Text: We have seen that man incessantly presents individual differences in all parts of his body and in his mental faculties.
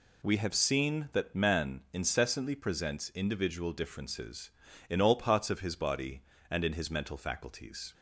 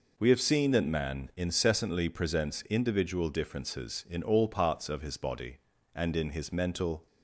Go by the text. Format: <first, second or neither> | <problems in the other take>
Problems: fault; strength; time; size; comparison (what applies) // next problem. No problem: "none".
first | stops before "faculties"; at 7.0 s